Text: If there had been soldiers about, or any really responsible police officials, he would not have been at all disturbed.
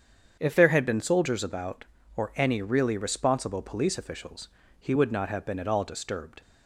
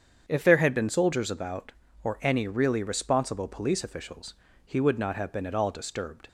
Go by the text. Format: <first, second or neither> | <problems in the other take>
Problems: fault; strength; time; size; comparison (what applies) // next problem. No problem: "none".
neither | starts louder than the rest; strong; the same in both